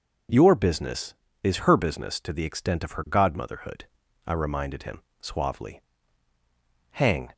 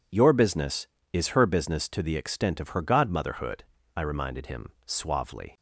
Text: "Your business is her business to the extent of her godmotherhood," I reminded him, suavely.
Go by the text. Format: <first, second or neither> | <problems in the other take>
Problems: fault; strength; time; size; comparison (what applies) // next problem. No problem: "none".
second | goes on to say "Hang"; slight; from 6.9 s on; 0.40 s long